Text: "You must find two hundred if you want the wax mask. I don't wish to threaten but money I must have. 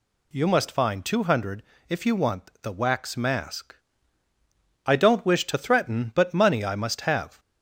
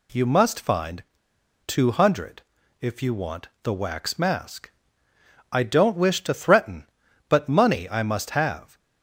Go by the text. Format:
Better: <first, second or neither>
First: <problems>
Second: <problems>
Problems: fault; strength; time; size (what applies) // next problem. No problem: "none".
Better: first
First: pauses between "hundred" and "if"; slight; at 1.6 s; 0.26 s long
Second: pauses between "find" and "two"; noticeable; at 1.0 s; 0.61 s long // pauses between "hundred" and "if"; at 2.4 s; 0.38 s long // pauses between "want" and "the"; slight; at 3.4 s; 0.16 s long